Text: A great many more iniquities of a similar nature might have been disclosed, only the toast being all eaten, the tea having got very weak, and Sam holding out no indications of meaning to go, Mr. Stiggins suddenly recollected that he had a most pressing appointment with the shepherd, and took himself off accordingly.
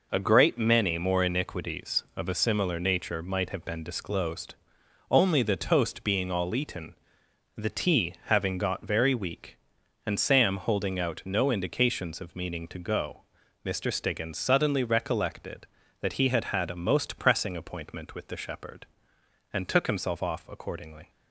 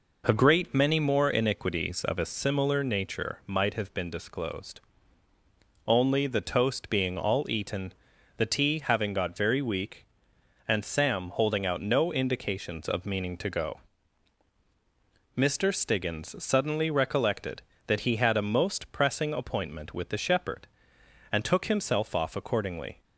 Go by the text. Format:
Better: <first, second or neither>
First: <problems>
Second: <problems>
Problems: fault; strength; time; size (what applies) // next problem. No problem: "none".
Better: second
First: says "had" twice; at 16.4 s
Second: none